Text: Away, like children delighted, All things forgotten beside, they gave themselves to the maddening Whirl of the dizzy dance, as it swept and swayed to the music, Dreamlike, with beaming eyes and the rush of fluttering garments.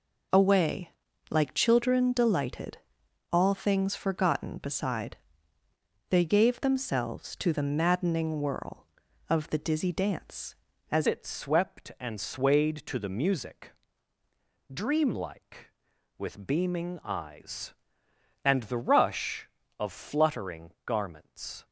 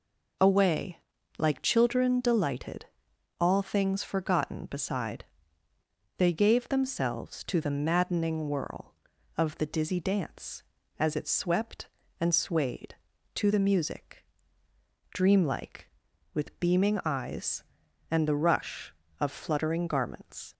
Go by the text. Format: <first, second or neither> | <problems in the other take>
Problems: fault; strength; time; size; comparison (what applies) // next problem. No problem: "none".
second | changes voice at "it"; from 11.0 s on; 10.6 s long